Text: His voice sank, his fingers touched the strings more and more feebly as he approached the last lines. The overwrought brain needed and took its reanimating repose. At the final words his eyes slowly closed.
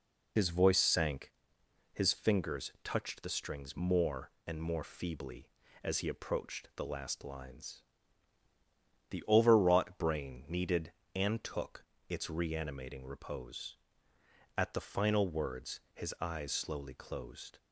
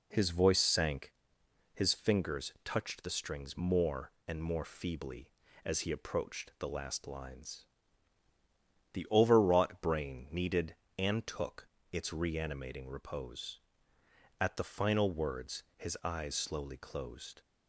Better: second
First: loses the start of "His"; at 0.3 s; 60 ms // pauses between "took" and "its"; slight; at 11.8 s; 0.24 s long // pauses between "words" and "his"; slight; at 15.7 s; 0.16 s long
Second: pauses between "took" and "its"; slight; at 11.6 s; 0.24 s long // pauses between "words" and "his"; slight; at 15.6 s; 0.16 s long

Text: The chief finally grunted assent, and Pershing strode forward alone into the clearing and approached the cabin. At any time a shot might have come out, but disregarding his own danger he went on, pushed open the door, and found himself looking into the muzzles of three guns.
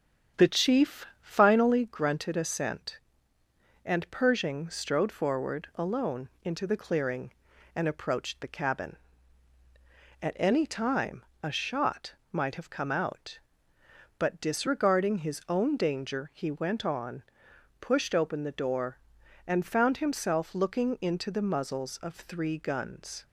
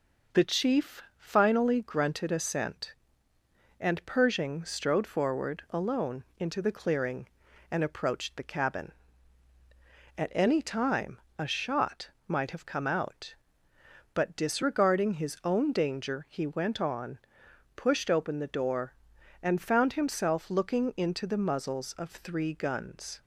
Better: second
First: starts louder than the rest; strong; until 1.8 s; 8 dB // pauses between "chief" and "finally"; slight; at 1.0 s; 0.16 s long // pauses between "time" and "a"; slight; at 11.2 s; 0.22 s long // pauses between "shot" and "might"; slight; at 12.1 s; 0.16 s long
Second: pauses between "chief" and "finally"; slight; at 1.0 s; 0.16 s long // pauses between "time" and "a"; slight; at 11.1 s; 0.22 s long // pauses between "shot" and "might"; slight; at 12.1 s; 0.16 s long

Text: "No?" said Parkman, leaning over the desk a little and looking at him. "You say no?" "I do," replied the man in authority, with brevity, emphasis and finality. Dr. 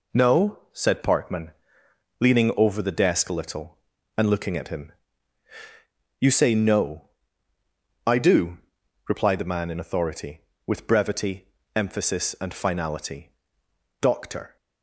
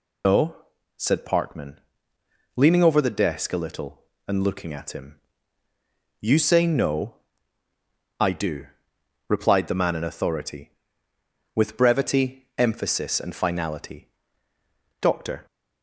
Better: first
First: none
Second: loses the start of "No"; at 0.2 s; 155 ms

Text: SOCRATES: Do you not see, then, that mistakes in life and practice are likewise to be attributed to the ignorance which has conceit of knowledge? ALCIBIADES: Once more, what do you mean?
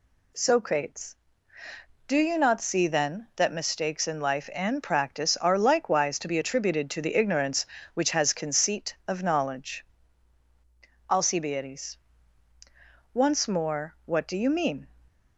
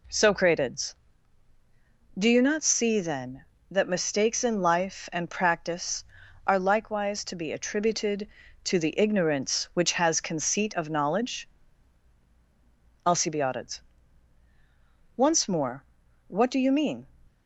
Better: neither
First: none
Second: none

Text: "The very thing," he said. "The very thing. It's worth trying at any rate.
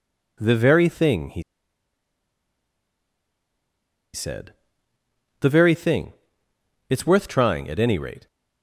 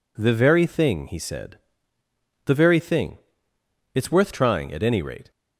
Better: second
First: pauses between "he" and "said"; strong; at 1.4 s; 2.7 s long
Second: none

